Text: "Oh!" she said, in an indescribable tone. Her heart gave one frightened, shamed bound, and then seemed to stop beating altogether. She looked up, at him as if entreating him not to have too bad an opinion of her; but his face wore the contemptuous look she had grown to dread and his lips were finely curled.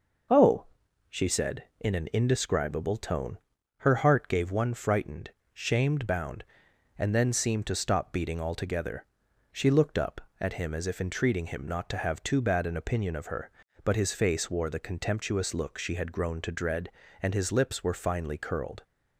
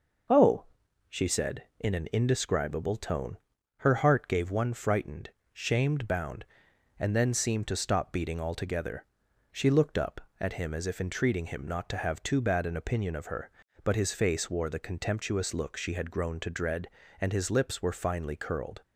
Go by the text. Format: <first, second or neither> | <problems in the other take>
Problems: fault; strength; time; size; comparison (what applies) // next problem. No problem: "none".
neither | none